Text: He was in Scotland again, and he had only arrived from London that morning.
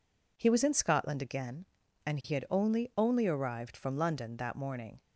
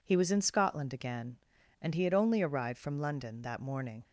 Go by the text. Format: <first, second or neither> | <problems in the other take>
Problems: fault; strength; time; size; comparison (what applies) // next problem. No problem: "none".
second | says "only" twice; at 2.9 s